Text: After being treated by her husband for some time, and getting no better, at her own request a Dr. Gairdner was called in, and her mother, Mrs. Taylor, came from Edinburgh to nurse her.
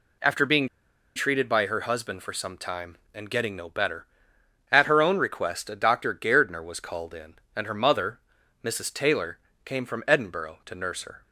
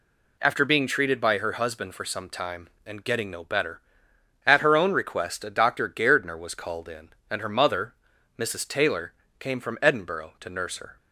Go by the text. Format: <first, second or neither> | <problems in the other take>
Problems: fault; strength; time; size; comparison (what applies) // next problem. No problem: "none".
second | pauses between "being" and "treated"; noticeable; at 0.6 s; 0.49 s long